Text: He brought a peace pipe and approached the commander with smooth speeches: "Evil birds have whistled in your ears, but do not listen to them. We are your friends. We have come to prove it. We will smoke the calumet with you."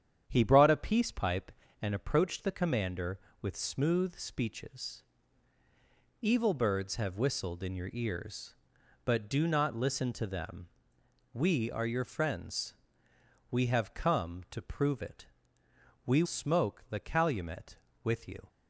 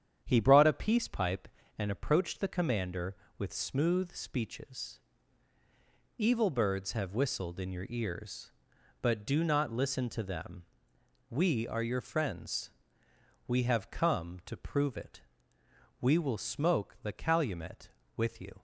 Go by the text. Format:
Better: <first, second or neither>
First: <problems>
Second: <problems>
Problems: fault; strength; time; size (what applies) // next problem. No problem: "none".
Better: second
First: starts louder than the rest; strong; until 1.2 s; 8.5 dB // skips "will"; at 16.2 s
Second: starts louder than the rest; strong; until 1.2 s; 8.5 dB